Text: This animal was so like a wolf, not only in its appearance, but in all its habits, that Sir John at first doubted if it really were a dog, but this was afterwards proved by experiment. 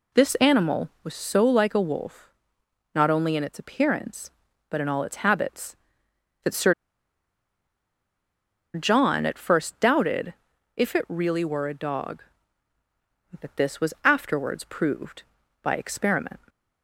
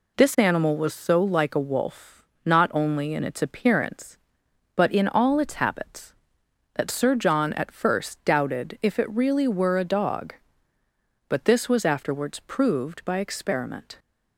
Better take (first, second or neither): second